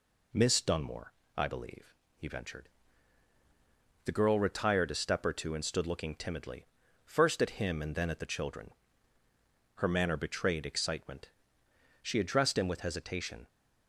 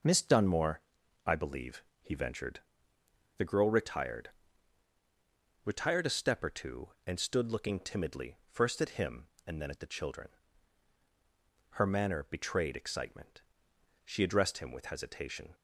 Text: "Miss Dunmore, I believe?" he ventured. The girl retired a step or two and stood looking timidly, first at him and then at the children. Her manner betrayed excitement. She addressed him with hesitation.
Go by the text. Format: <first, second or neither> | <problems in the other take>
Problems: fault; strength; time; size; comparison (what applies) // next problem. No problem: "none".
first | says "retired" twice; at 5.6 s